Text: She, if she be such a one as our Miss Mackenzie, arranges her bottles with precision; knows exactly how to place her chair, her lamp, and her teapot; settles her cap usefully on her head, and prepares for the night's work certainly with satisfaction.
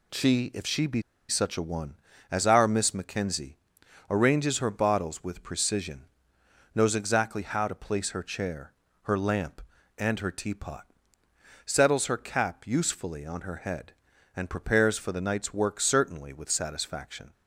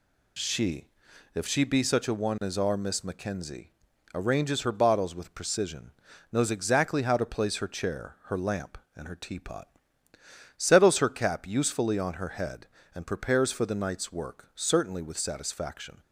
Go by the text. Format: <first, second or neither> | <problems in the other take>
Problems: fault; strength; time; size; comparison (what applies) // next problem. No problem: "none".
second | pauses between "be" and "such"; slight; at 1.0 s; 0.27 s long